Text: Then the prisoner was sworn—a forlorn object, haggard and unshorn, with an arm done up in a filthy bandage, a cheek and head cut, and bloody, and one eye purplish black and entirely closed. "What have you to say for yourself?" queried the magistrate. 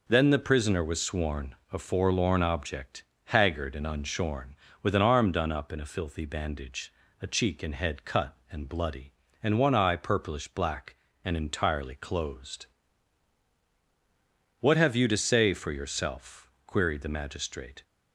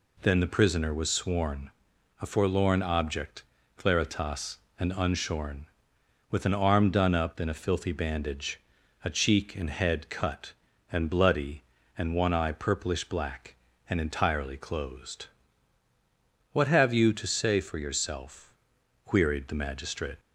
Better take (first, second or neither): first